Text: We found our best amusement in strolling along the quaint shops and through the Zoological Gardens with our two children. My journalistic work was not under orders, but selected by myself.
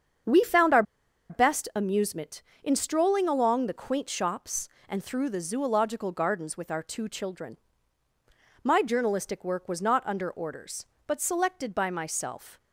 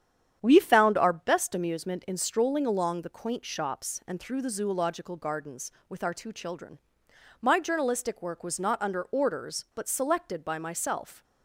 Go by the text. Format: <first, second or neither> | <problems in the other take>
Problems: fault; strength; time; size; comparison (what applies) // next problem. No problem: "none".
second | starts louder than the rest; strong; until 1.8 s; 7.5 dB; strong in the second // pauses between "our" and "best"; noticeable; at 0.8 s; 0.47 s long